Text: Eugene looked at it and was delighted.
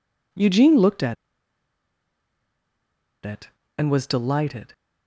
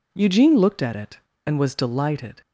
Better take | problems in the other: second | pauses between "at" and "it"; strong; at 1.1 s; 2.1 s long

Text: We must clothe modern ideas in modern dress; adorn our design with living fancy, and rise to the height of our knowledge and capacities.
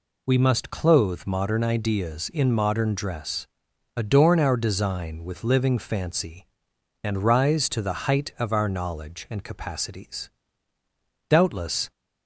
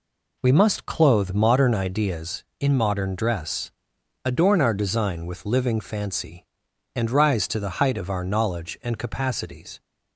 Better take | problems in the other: second | goes on to say "Doubtless"; noticeable; from 11.2 s on; 0.62 s long

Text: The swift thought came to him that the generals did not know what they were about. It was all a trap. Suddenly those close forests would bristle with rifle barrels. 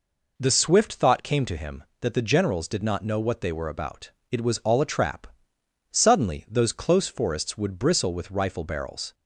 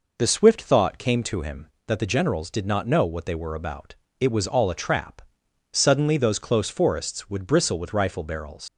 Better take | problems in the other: first | leaves "barrels" unfinished; at 8.6 s; 85 ms

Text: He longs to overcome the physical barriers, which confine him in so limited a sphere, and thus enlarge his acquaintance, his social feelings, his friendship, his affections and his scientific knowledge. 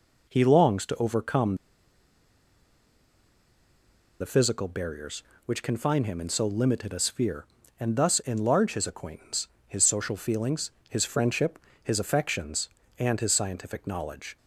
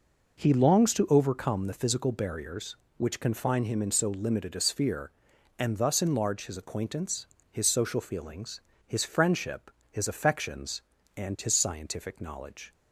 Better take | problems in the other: second | pauses between "overcome" and "the"; strong; at 1.5 s; 2.6 s long

